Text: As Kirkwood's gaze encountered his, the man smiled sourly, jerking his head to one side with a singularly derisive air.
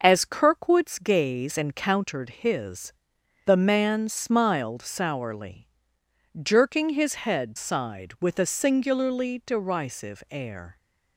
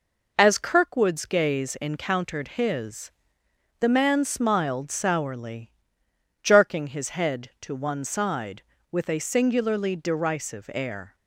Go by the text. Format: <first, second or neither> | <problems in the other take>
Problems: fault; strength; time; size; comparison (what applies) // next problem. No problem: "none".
second | skips "to one"; at 7.5 s